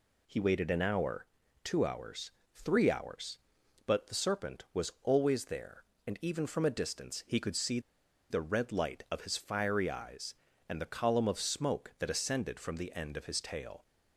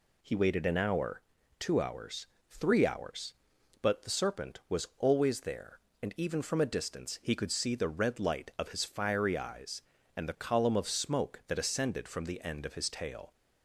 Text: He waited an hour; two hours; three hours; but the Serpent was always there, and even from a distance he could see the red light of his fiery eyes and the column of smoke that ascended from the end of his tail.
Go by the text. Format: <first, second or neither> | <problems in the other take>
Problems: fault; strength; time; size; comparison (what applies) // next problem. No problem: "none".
second | pauses between "see" and "the"; noticeable; at 7.7 s; 0.51 s long